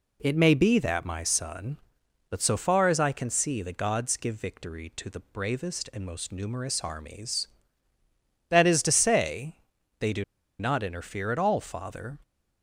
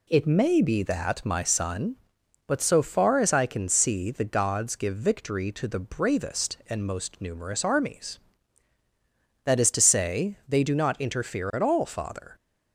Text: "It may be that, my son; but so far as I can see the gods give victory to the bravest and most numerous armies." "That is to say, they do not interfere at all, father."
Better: second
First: pauses between "do" and "not"; at 10.2 s; 0.36 s long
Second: none

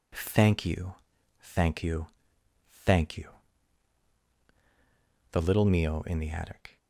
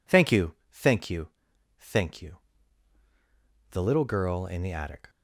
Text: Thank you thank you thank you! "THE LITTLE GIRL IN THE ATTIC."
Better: second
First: pauses between "you" and "thank"; noticeable; at 0.9 s; 0.62 s long // pauses between "you" and "thank"; noticeable; at 2.0 s; 0.78 s long // says "Mio" for "GIRL"; at 5.6 s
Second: pauses between "you" and "thank"; slight; at 0.5 s; 0.18 s long // pauses between "you" and "thank"; noticeable; at 1.2 s; 0.50 s long

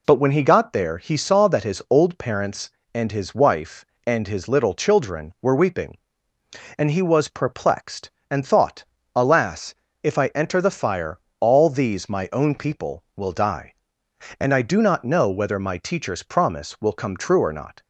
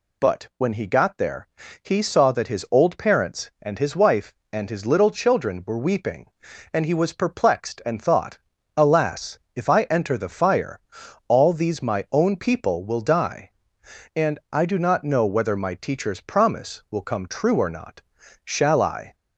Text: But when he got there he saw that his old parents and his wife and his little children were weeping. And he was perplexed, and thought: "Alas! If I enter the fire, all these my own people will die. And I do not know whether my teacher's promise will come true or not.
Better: first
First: none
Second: pauses between "there" and "he"; slight; at 1.4 s; 0.34 s long // goes on to say "Shall I"; noticeable; from 18.4 s on; 0.70 s long

